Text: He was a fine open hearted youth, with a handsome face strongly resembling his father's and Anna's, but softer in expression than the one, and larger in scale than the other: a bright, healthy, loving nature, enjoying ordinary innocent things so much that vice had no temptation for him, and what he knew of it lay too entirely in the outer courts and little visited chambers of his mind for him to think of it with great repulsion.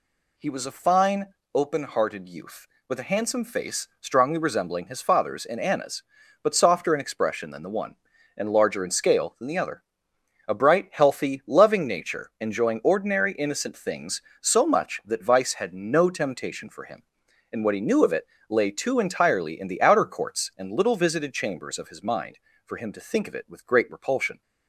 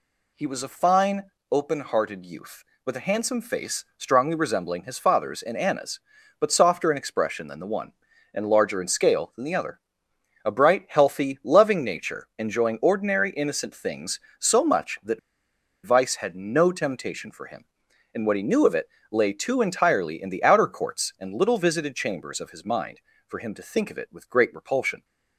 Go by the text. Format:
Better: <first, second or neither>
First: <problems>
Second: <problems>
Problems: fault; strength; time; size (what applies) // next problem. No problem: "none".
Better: first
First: pauses between "fine" and "open"; slight; at 1.2 s; 0.26 s long // pauses between "it" and "lay"; slight; at 18.2 s; 0.24 s long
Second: pauses between "fine" and "open"; slight; at 1.2 s; 0.26 s long // pauses between "that" and "vice"; noticeable; at 15.1 s; 0.66 s long // pauses between "it" and "lay"; slight; at 18.8 s; 0.24 s long